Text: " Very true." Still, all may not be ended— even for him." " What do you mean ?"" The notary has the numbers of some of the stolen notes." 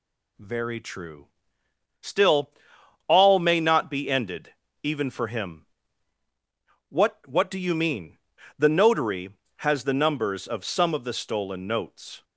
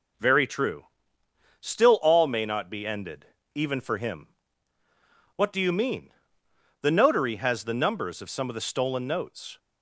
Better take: second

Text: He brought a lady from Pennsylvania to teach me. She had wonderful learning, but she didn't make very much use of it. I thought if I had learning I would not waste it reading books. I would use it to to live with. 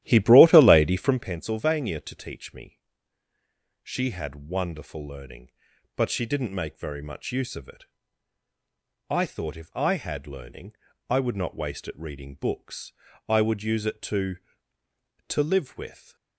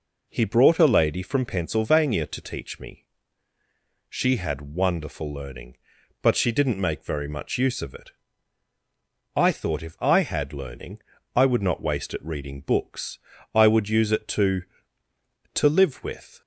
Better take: second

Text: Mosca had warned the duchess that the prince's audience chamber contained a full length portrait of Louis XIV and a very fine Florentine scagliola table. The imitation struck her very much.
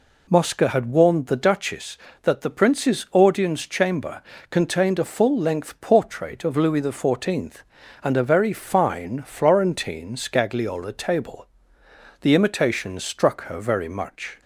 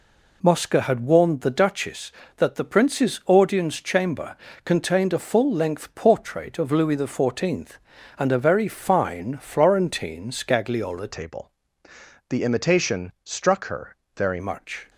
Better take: first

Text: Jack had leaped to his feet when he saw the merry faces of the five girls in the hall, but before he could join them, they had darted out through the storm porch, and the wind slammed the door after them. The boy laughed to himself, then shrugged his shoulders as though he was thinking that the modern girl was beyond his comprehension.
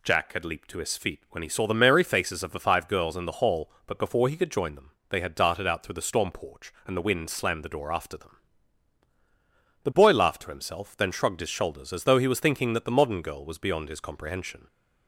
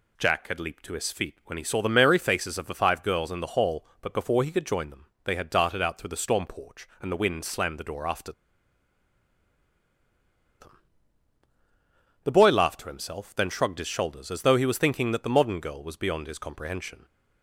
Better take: first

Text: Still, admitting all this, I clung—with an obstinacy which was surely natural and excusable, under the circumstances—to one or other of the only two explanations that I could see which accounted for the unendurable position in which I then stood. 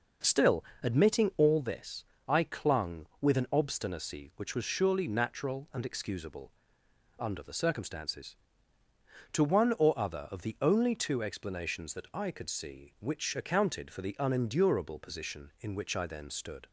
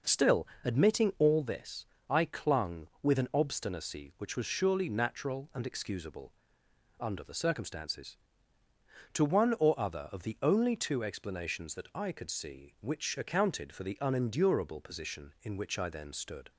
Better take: neither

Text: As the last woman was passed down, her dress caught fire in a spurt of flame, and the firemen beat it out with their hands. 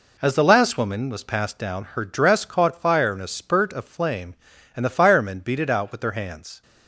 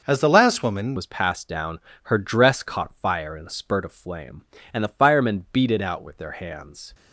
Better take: first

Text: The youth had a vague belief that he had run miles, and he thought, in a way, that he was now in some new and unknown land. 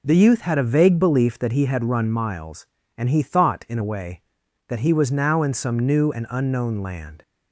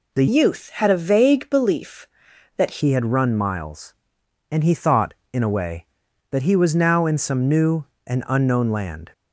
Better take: first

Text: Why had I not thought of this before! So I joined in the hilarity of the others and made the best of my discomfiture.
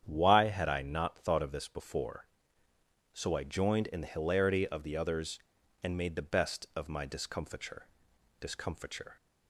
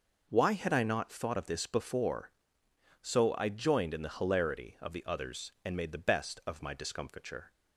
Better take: second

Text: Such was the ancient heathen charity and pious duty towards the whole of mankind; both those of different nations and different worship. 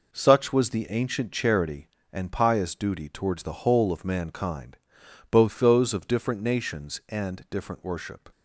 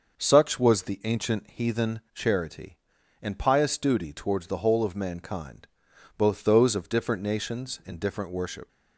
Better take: second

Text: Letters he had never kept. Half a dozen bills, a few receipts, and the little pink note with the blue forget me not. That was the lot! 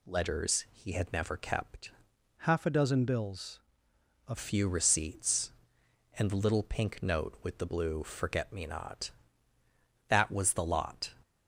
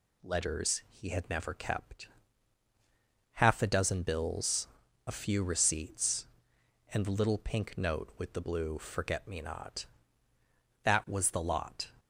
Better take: second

